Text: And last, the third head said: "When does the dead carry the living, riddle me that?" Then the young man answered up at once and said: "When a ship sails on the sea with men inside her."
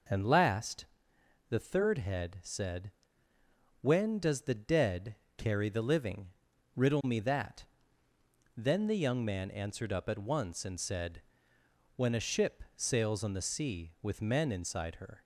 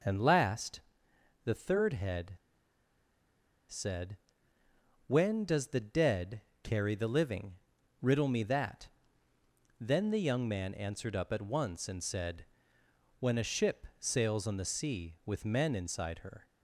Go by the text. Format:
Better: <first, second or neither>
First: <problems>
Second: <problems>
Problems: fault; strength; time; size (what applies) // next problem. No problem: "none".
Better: first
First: pauses between "dead" and "carry"; slight; at 5.1 s; 0.22 s long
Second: pauses between "head" and "said"; strong; at 2.3 s; 1.3 s long // pauses between "dead" and "carry"; slight; at 6.4 s; 0.22 s long